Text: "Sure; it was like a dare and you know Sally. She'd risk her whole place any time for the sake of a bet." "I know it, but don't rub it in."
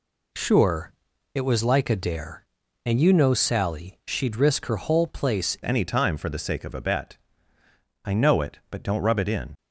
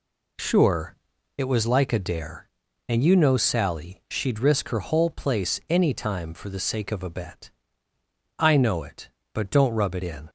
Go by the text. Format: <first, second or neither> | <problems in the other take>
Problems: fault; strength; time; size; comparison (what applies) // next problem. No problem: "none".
second | changes voice at "any"; from 5.6 s on; 3.9 s long